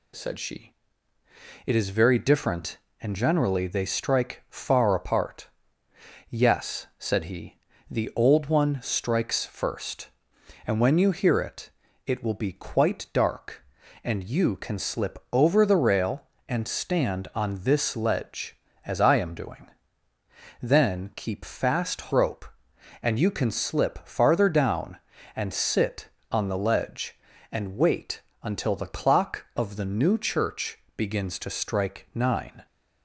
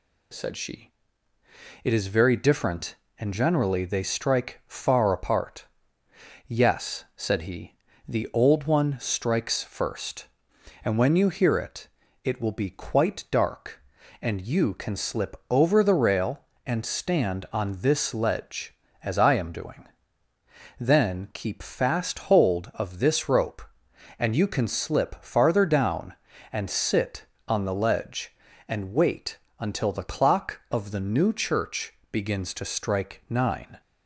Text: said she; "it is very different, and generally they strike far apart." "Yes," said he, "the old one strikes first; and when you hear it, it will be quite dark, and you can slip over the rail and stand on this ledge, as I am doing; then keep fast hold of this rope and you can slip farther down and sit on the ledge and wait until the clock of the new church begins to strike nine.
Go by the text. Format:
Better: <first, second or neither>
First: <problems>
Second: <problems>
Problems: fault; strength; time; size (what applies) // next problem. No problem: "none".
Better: second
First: skips "hold of this"; at 22.1 s // pauses between "wait" and "until"; slight; at 28.2 s; 0.20 s long // pauses between "church" and "begins"; slight; at 30.7 s; 0.18 s long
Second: pauses between "wait" and "until"; slight; at 29.3 s; 0.20 s long // pauses between "church" and "begins"; slight; at 31.9 s; 0.18 s long